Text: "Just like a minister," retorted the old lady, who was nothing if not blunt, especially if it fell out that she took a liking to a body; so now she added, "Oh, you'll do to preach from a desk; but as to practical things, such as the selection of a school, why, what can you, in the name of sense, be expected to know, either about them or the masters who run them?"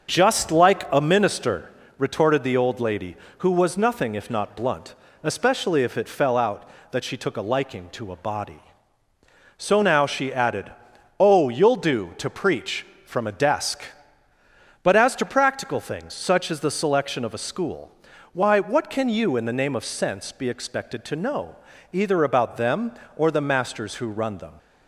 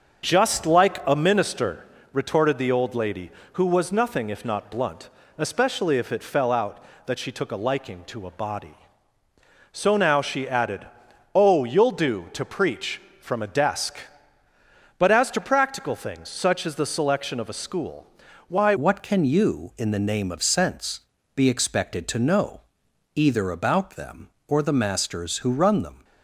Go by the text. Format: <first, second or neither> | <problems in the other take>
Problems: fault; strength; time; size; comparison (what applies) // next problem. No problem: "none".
first | starts louder than the rest; until 1.2 s; 6.5 dB; also in the first // changes voice at "what"; from 18.7 s on; 7.3 s long